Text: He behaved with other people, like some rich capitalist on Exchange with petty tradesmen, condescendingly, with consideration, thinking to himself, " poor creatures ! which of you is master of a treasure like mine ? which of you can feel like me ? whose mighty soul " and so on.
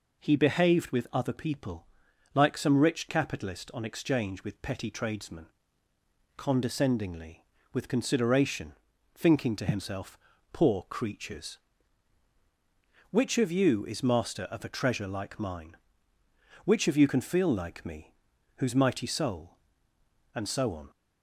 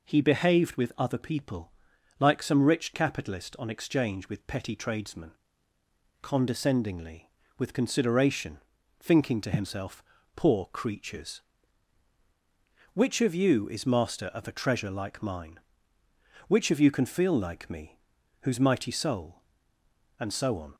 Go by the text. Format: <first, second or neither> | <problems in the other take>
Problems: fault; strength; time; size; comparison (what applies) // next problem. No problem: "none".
neither | none